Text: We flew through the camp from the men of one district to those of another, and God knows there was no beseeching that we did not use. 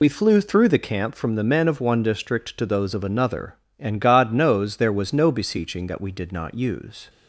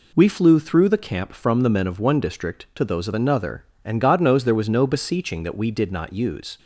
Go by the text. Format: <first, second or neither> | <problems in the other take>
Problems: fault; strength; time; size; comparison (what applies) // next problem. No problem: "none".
second | loses the start of "We"; at 0.0 s; 45 ms